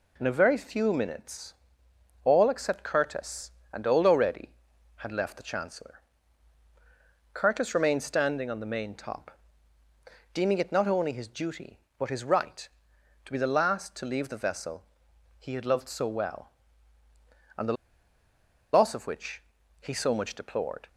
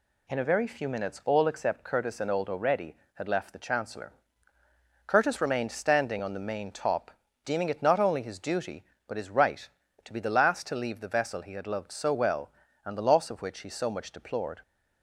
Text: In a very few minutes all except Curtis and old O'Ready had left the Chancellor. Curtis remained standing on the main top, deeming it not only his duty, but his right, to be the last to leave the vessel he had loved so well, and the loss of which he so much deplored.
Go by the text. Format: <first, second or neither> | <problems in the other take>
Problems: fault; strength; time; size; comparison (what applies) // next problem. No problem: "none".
second | pauses between "minutes" and "all"; noticeable; at 1.5 s; 0.72 s long // pauses between "vessel" and "he"; noticeable; at 14.8 s; 0.54 s long // pauses between "the" and "loss"; at 17.7 s; 1.0 s long // pauses between "which" and "he"; at 19.3 s; 0.40 s long